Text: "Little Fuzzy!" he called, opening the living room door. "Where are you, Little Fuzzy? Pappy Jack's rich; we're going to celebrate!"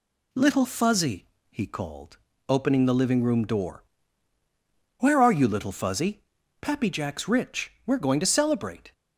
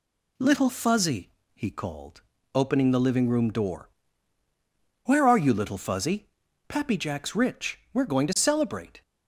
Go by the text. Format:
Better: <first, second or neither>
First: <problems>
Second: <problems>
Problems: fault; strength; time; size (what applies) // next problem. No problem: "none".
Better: neither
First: none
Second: none